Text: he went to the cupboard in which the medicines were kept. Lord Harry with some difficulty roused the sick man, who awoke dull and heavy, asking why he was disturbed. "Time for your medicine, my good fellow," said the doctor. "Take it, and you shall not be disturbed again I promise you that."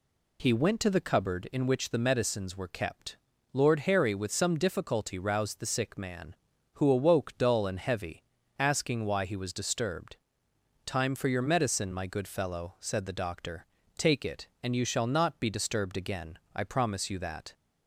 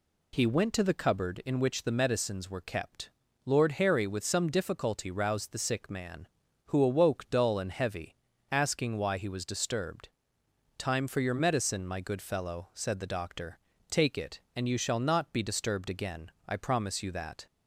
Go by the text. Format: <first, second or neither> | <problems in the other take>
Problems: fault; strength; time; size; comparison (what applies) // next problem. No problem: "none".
neither | pauses between "again" and "I"; slight; the same in both